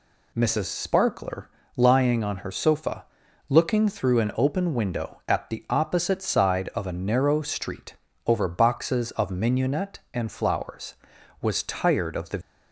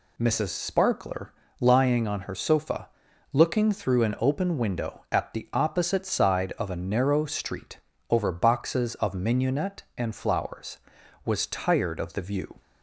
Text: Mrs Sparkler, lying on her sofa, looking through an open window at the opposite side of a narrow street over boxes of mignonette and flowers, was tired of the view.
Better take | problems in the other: second | pauses between "street" and "over"; slight; at 7.9 s; 0.32 s long; slight in the second // stops before "view"; at 12.4 s

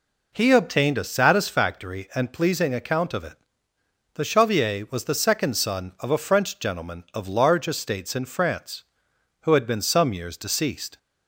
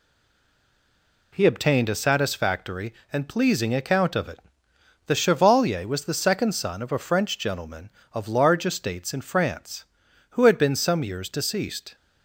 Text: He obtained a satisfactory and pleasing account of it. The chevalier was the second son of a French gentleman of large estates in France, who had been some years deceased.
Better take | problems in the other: first | stays silent before the first word; noticeable; until 1.3 s; 1.3 s long

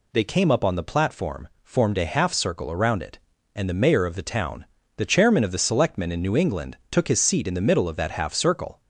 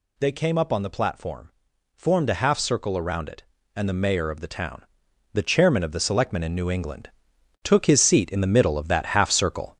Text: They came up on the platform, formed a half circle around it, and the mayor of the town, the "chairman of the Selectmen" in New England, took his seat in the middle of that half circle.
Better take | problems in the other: first | gets louder; noticeable; throughout; 4.5 dB

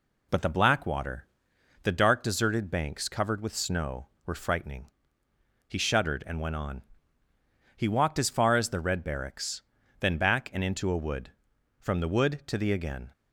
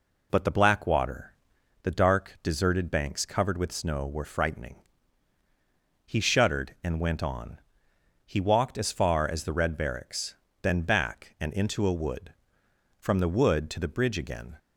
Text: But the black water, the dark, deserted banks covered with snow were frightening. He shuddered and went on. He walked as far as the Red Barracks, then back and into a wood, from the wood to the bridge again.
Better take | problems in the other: second | skips "bridge"; at 12.7 s

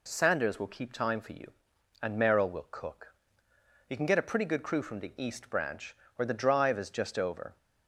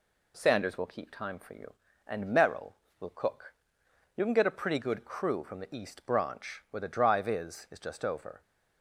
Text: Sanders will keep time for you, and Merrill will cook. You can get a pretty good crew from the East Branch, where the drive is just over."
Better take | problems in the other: first | says "is" twice; at 7.7 s

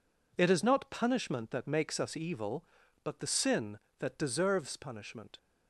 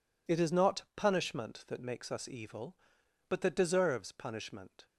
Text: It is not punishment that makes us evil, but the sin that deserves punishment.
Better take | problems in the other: first | skips "the sin"; at 3.4 s

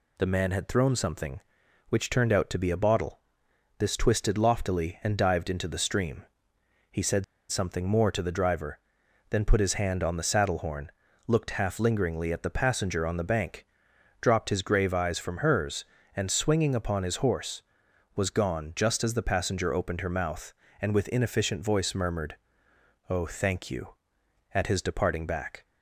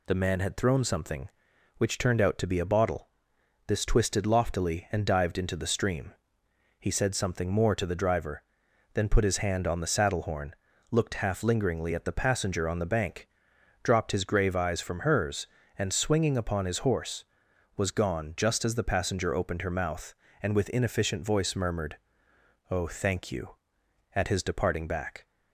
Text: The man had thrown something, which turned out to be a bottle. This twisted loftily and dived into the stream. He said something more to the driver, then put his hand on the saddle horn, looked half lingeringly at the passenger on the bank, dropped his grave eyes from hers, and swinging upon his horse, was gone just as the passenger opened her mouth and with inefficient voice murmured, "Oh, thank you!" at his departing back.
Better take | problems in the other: second | pauses between "said" and "something"; slight; at 7.2 s; 0.26 s long

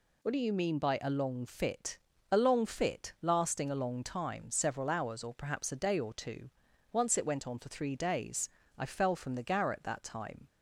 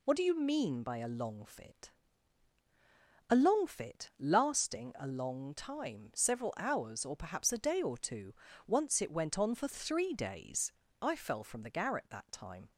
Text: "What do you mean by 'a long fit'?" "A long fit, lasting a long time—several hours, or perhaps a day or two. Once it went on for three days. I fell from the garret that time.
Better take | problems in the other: neither | none

